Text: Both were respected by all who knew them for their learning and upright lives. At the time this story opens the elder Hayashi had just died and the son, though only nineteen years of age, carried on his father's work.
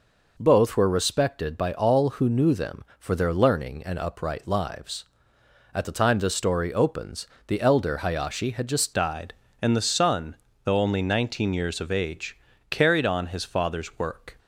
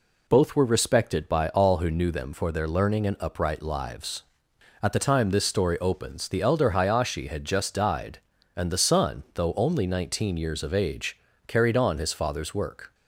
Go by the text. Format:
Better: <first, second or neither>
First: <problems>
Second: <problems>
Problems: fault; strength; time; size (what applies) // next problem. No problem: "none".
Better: second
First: pauses between "opens" and "the"; slight; at 7.2 s; 0.20 s long // changes voice at "died"; from 8.9 s on; 5.4 s long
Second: none